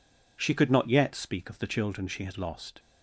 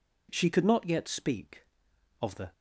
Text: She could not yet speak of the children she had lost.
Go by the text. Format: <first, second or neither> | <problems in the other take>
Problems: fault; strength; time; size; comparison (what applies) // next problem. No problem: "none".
first | stops before "children she had lost"; at 2.5 s